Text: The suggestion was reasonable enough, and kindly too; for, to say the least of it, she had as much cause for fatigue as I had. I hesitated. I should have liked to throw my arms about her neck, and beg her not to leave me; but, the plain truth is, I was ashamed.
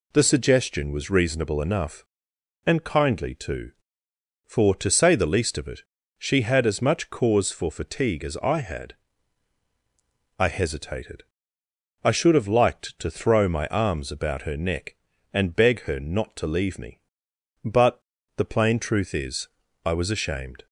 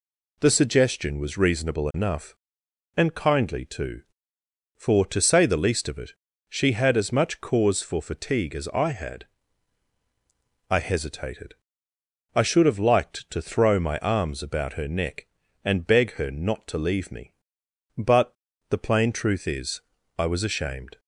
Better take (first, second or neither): neither